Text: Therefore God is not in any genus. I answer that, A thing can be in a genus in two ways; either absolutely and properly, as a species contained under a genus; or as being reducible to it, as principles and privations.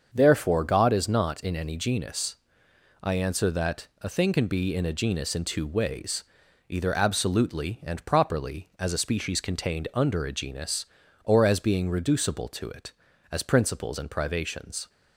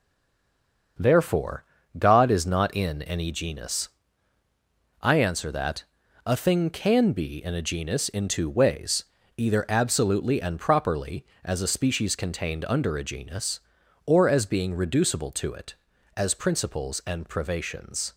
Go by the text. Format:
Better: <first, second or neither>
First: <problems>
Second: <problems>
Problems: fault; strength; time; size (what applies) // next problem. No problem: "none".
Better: first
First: starts louder than the rest; until 1.1 s; 6.5 dB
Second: stays silent before the first word; slight; until 0.9 s; 0.9 s long // starts louder than the rest; until 2.3 s; 6.5 dB // pauses between "Therefore" and "God"; slight; at 1.6 s; 0.34 s long